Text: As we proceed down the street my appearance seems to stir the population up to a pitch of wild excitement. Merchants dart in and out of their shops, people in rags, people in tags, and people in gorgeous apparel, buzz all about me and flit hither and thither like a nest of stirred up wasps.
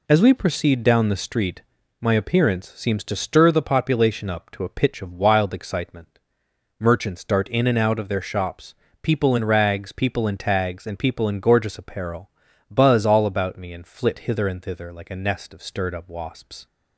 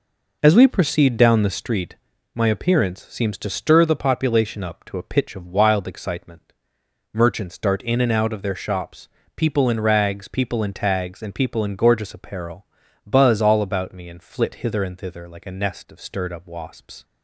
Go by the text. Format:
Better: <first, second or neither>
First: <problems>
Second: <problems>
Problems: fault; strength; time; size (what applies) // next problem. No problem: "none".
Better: first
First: pauses between "street" and "my"; at 1.6 s; 0.38 s long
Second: starts louder than the rest; noticeable; until 1.6 s; 4.5 dB // pauses between "street" and "my"; at 1.9 s; 0.38 s long